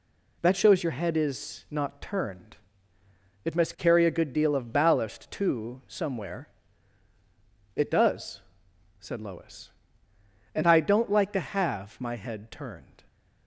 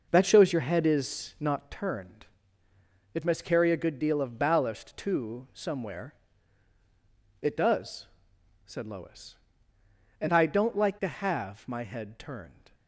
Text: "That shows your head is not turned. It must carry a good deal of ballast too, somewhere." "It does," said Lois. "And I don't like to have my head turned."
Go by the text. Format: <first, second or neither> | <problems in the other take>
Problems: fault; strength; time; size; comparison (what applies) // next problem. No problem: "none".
first | starts louder than the rest; noticeable; until 1.6 s; 5.5 dB